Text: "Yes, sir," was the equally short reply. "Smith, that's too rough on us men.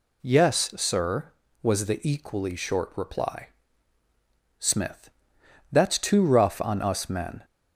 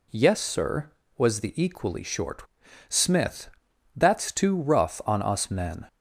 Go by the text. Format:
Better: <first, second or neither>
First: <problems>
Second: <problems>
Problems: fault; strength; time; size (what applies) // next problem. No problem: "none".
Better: first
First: none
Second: skips "reply"; at 2.6 s